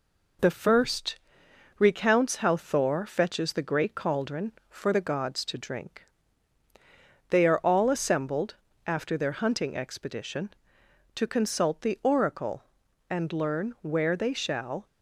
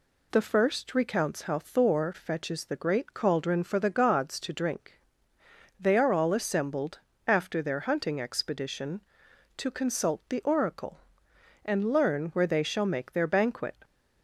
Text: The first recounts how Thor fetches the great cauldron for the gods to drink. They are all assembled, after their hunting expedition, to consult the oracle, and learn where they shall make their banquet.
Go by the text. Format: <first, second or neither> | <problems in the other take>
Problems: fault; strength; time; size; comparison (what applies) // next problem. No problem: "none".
second | pauses between "first" and "recounts"; noticeable; at 1.1 s; 0.60 s long // stops before "make their banquet"; at 14.8 s